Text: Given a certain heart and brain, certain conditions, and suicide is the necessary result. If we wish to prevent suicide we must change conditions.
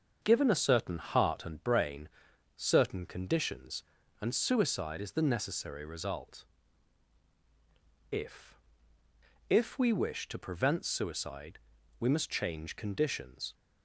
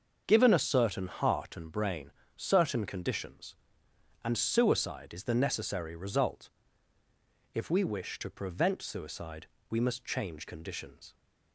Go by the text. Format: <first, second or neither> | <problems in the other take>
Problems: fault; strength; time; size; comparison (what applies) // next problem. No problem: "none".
second | starts louder than the rest; until 1.2 s; 6.5 dB; also in the second // says "If" twice; at 9.4 s // pauses between "suicide" and "we"; at 11.5 s; 0.42 s long; slight in the second